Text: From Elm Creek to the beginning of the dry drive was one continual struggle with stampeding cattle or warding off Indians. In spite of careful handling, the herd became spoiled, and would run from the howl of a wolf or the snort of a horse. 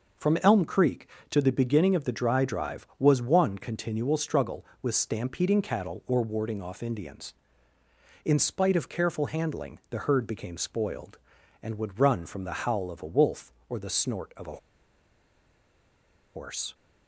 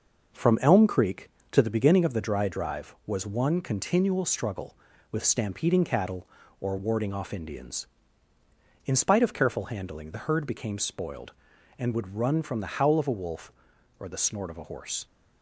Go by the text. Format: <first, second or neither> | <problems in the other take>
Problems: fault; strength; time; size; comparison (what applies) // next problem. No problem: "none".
second | pauses between "a" and "horse"; strong; at 14.5 s; 1.7 s long